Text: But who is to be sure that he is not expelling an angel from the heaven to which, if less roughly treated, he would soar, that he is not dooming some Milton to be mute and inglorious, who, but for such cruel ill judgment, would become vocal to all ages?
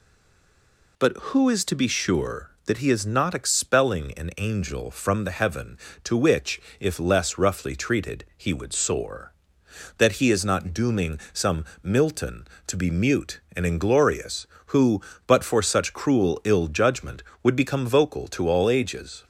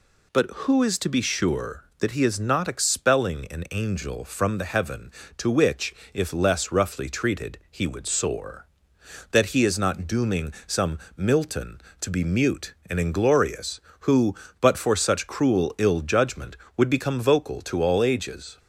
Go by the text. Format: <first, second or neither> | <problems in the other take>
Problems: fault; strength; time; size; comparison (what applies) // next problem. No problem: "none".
second | stays silent before the first word; until 0.9 s; 0.9 s long // pauses between "some" and "Milton"; slight; at 11.6 s; 0.18 s long; slight in the second